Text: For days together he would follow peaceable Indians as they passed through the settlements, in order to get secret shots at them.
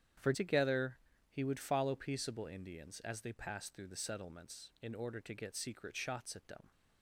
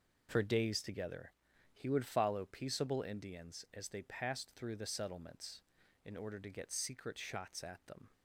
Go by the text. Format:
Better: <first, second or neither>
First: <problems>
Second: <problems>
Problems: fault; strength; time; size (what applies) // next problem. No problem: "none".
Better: second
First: starts louder than the rest; strong; until 1.5 s; 9.5 dB // skips "days"; at 0.3 s // pauses between "together" and "he"; slight; at 0.9 s; 0.32 s long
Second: pauses between "together" and "he"; at 1.3 s; 0.42 s long